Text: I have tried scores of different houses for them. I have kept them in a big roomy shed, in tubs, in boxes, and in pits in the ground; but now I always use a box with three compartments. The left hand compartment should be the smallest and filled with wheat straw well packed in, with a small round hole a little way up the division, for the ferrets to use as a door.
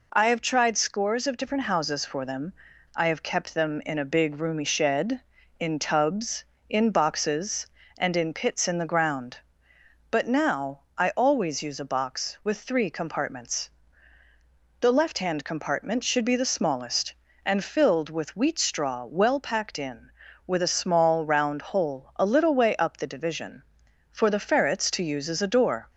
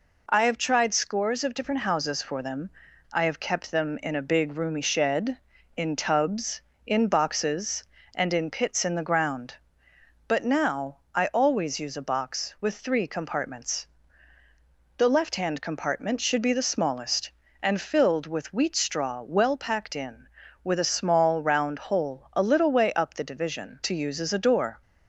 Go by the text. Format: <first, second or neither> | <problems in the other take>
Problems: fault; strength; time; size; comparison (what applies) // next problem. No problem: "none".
first | pauses between "now" and "I"; slight; at 10.9 s; 0.16 s long; slight in the first // skips "for the ferrets"; at 23.8 s